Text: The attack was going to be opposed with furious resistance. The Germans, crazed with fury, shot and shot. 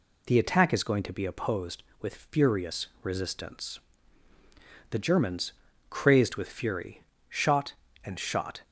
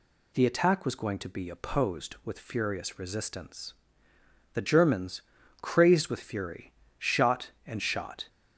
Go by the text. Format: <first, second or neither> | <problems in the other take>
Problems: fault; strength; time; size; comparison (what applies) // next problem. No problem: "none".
second | says "is" for "was"; at 0.7 s